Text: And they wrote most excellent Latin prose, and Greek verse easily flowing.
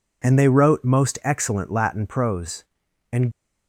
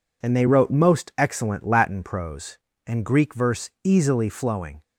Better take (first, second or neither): second